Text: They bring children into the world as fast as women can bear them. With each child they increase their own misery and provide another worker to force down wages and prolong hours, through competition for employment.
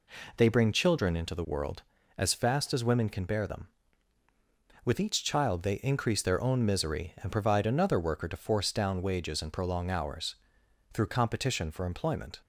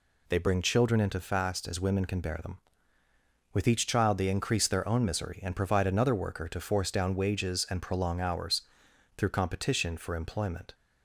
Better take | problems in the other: first | skips "the world as"; at 1.1 s

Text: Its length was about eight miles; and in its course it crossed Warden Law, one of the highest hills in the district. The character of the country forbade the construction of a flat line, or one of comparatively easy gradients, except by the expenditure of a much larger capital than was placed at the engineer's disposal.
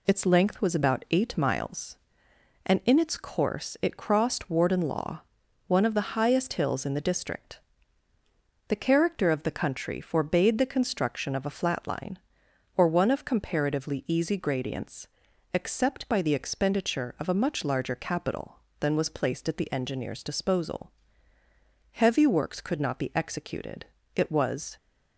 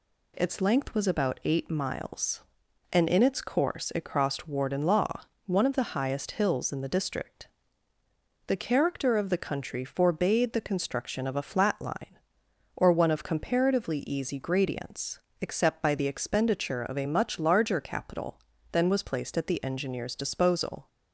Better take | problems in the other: second | goes on to say "Heavy works could not be executed it was"; strong; from 21.9 s on; 2.8 s long

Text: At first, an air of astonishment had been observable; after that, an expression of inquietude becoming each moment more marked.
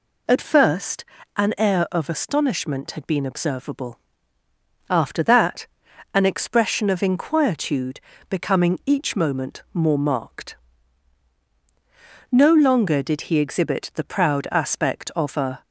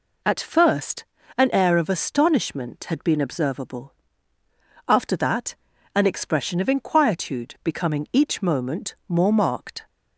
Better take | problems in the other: second | pauses between "inquietude" and "becoming"; slight; at 7.9 s; 0.28 s long // goes on to say "No longer did he exhibit the proud aspect of a"; strong; from 12.3 s on; 3.3 s long

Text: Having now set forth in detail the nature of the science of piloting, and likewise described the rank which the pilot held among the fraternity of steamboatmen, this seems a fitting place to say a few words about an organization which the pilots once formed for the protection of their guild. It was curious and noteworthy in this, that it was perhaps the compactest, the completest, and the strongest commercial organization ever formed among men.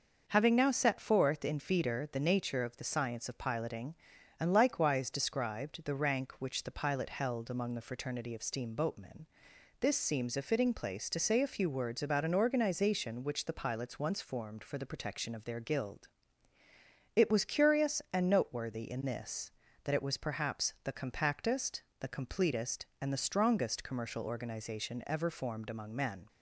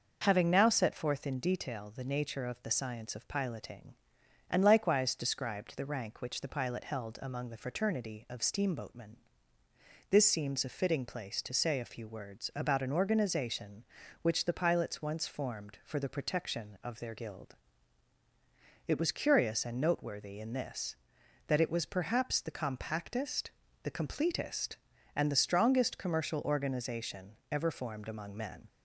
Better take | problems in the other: second | starts louder than the rest; noticeable; until 1.2 s; 6 dB // says "feeder" for "detail"; at 1.5 s

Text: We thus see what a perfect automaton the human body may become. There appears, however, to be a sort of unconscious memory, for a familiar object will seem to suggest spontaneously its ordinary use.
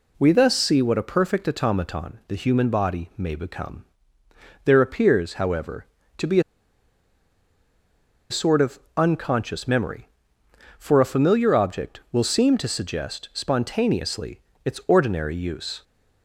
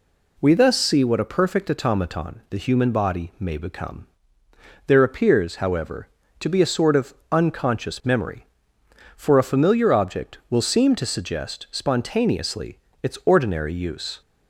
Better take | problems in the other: second | pauses between "be" and "a"; strong; at 6.3 s; 1.9 s long // pauses between "of" and "unconscious"; slight; at 8.7 s; 0.20 s long; slight in the second // pauses between "spontaneously" and "its"; slight; at 14.4 s; 0.24 s long; slight in the second

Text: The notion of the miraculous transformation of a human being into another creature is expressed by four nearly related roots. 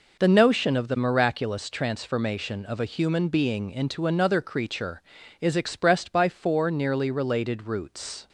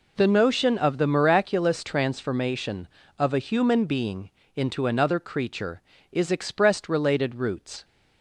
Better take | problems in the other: first | pauses between "being" and "into"; slight; at 4.3 s; 0.24 s long // skips "by four nearly"; at 6.8 s

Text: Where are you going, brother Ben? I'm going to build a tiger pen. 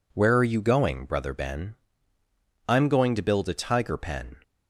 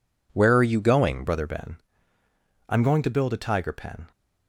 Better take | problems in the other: first | changes voice at "brother"; from 1.2 s on; 2.9 s long

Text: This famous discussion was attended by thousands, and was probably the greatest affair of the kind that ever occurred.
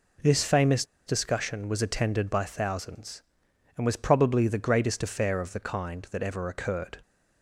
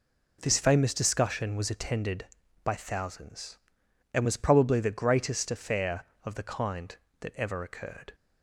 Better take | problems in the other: second | pauses between "famous" and "discussion"; slight; at 0.8 s; 0.23 s long

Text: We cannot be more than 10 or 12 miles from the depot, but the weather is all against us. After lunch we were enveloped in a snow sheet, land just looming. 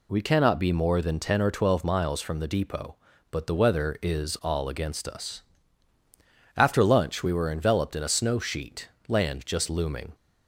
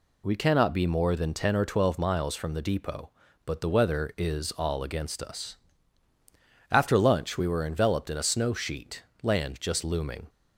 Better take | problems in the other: neither | none

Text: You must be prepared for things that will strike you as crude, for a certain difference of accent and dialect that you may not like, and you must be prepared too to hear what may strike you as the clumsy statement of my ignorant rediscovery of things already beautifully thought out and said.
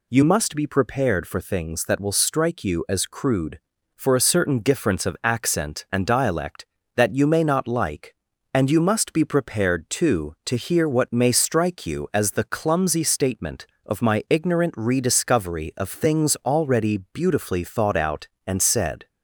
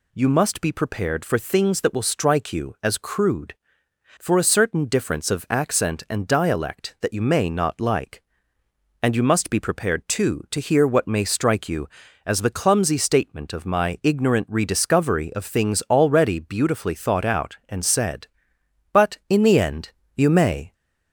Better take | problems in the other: first | goes on to say "But in the end you may"; strong; from 18.9 s on; 1.7 s long

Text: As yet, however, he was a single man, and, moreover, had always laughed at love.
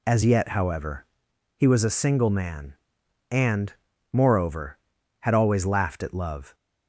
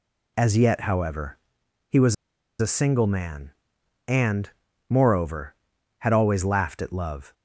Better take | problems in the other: first | pauses between "was" and "a"; noticeable; at 2.1 s; 0.45 s long

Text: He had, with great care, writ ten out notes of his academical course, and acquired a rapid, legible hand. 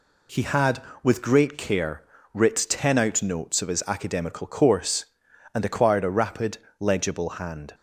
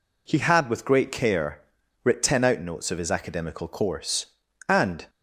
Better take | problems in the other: first | stops before "acquired a rapid legible hand"; at 5.0 s

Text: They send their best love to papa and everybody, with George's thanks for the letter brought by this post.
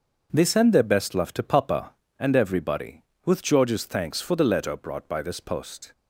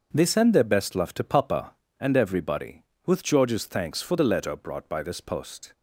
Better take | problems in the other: neither | starts louder than the rest; the same in both

